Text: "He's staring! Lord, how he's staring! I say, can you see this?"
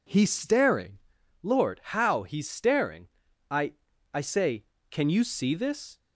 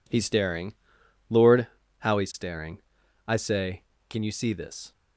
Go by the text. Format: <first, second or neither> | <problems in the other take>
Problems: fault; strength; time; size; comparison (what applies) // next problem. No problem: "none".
second | says "I" twice; at 4.1 s